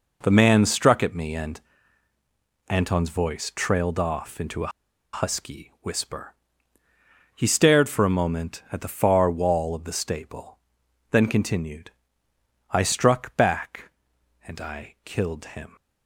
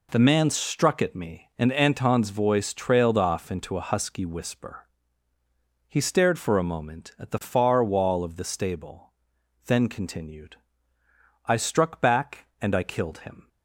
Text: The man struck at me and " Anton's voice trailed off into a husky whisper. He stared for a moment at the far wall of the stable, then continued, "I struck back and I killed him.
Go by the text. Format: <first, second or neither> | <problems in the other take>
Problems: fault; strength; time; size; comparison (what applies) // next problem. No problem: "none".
second | pauses between "a" and "husky"; at 4.7 s; 0.44 s long